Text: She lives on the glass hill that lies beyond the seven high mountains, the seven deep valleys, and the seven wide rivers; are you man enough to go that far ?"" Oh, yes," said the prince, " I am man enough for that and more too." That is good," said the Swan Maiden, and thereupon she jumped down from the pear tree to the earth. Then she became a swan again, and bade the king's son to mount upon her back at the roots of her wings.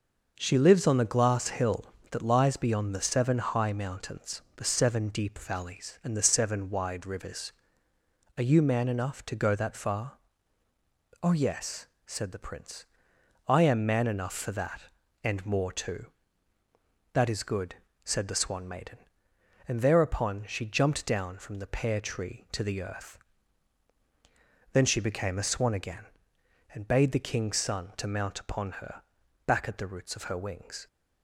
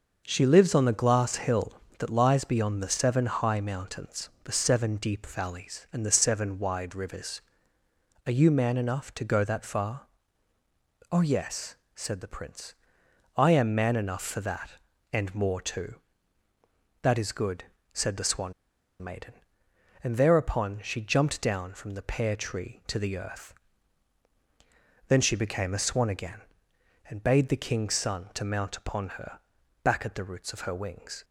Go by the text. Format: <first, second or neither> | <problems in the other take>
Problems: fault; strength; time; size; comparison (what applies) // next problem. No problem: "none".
first | starts louder than the rest; until 1.2 s; 6 dB; also in the first // pauses between "Swan" and "Maiden"; noticeable; at 18.5 s; 0.48 s long // pauses between "her" and "back"; at 29.3 s; 0.42 s long; also in the first